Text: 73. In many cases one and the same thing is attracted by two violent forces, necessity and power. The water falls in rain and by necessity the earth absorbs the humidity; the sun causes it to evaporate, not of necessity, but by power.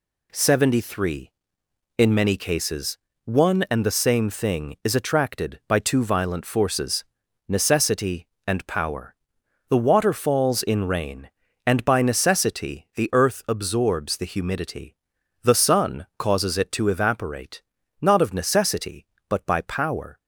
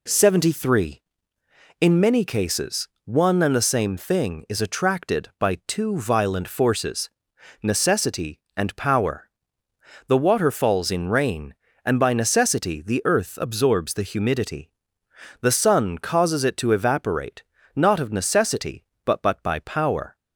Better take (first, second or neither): first